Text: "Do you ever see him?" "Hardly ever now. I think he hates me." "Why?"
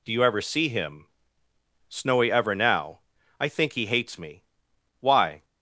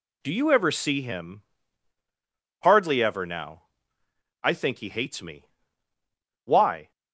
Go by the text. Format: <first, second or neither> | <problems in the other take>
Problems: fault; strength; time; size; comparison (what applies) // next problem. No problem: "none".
second | says "Snowy" for "Hardly"; at 1.8 s